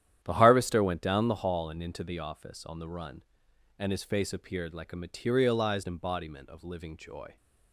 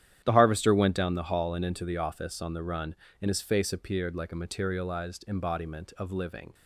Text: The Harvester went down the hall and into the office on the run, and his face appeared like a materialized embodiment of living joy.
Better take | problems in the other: first | starts louder than the rest; strong; until 1.2 s; 11 dB; strong in the first // stops before "joy"; at 6.5 s

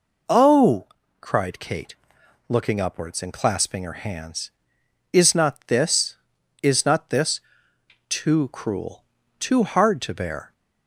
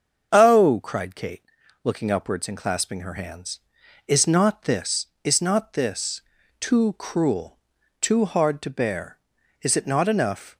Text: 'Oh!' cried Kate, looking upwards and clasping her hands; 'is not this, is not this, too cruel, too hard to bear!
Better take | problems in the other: first | starts louder than the rest; until 1.3 s; 7 dB // goes on to say "Is it not enough"; noticeable; from 9.6 s on; 0.96 s long

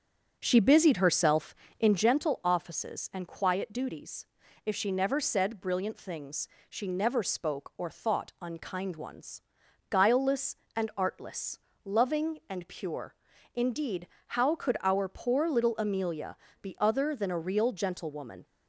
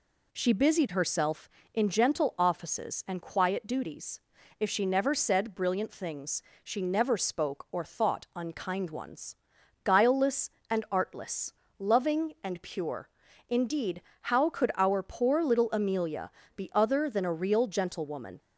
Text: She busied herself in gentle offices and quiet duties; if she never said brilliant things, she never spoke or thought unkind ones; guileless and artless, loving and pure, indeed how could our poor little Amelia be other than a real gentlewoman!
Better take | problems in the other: second | starts louder than the rest; strong; until 2.2 s; 7.5 dB // pauses between "indeed" and "how"; slight; at 14.0 s; 0.20 s long; slight in the second // pauses between "Amelia" and "be"; slight; at 16.3 s; 0.26 s long; slight in the second

